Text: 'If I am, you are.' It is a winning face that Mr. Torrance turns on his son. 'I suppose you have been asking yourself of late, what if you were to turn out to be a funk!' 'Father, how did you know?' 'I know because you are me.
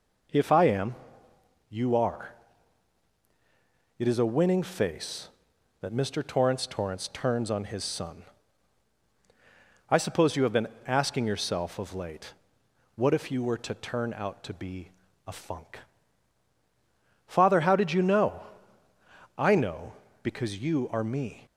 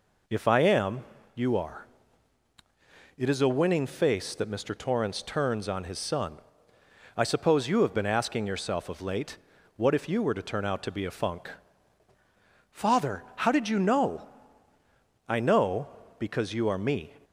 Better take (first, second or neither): second